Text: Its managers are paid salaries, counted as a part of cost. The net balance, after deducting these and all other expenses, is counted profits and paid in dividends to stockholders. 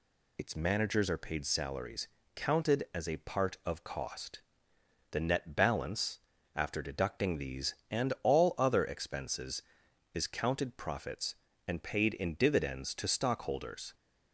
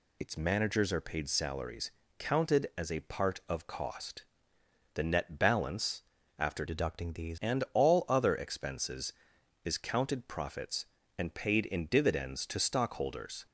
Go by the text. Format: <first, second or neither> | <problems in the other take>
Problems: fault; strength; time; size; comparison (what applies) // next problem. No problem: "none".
first | changes voice from "deducting" to "these"; from 6.6 to 7.3 s; 0.7 s long